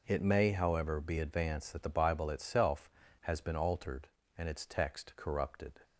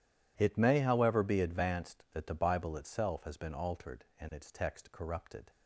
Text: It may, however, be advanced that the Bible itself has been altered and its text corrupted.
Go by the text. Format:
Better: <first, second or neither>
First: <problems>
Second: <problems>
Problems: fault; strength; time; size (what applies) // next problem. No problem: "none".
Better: neither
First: none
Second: none